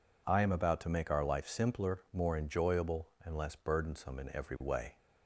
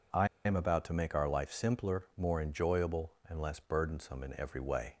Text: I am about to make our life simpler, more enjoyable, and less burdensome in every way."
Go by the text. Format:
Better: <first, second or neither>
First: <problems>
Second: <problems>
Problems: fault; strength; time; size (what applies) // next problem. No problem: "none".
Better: first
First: none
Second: pauses between "I" and "am"; slight; at 0.2 s; 0.18 s long